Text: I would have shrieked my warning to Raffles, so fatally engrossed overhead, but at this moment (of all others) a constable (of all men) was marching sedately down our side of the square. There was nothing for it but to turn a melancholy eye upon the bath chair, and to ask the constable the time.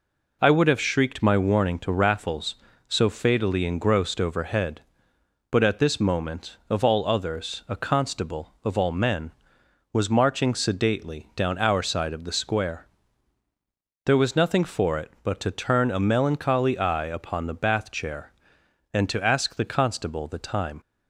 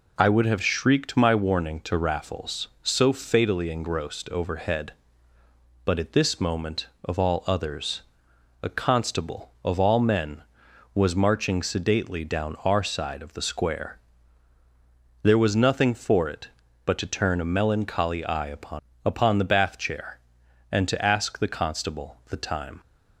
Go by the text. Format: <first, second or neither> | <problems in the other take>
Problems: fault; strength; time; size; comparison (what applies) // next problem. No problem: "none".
first | says "upon" twice; at 19.0 s